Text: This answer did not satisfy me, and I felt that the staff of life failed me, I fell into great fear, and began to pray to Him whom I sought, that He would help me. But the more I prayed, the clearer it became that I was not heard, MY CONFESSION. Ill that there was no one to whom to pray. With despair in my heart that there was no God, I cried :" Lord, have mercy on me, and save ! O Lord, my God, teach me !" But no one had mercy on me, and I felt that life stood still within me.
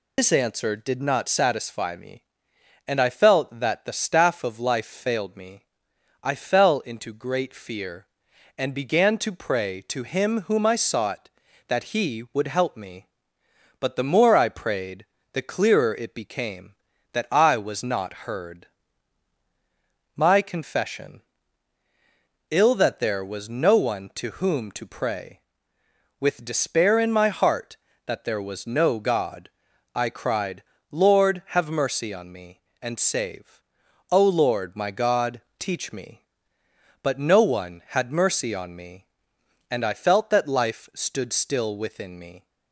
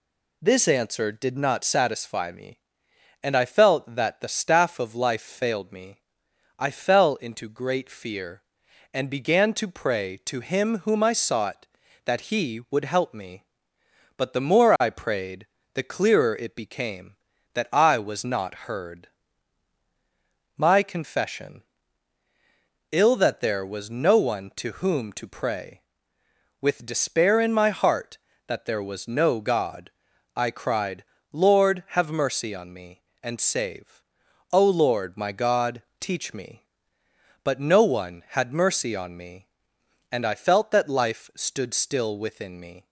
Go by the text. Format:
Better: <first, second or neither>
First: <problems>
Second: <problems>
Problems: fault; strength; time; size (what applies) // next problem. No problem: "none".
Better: second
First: loses the start of "This"; at 0.1 s; 125 ms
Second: none